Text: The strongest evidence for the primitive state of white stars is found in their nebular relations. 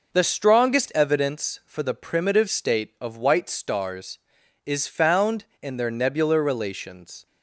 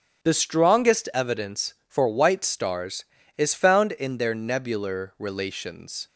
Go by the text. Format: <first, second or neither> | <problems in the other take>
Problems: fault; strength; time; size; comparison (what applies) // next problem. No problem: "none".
first | starts louder than the rest; strong; until 1.3 s; 7.5 dB // skips "the primitive state of"; at 2.0 s